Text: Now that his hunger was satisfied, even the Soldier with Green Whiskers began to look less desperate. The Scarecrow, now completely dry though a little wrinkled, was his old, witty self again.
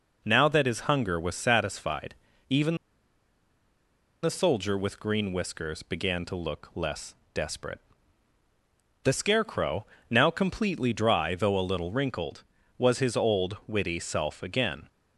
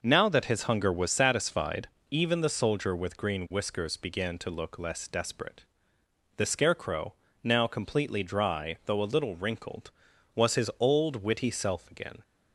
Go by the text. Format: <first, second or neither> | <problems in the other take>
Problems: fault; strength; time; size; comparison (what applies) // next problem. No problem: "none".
second | pauses between "even" and "the"; strong; at 2.7 s; 1.4 s long // pauses between "less" and "desperate"; slight; at 7.1 s; 0.20 s long